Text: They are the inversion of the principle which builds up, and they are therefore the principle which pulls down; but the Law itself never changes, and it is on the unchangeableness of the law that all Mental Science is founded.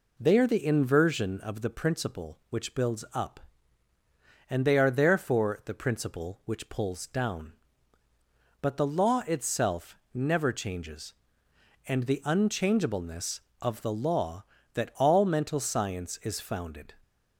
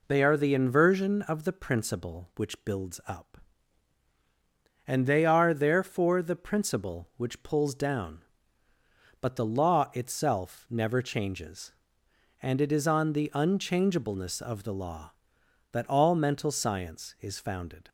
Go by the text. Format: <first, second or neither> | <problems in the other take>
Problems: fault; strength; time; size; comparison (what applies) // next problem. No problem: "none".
second | pauses between "itself" and "never"; slight; at 9.9 s; 0.20 s long // skips "it is on"; at 12.0 s